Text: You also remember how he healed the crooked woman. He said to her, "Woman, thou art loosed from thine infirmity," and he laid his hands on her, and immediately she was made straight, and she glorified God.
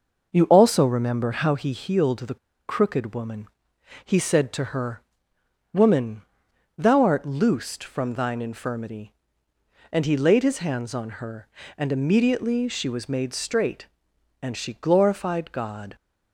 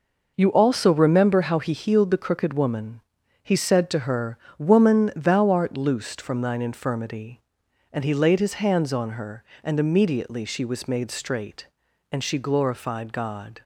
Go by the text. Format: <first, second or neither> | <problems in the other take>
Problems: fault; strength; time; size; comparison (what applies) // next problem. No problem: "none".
second | pauses between "the" and "crooked"; slight; at 2.3 s; 0.31 s long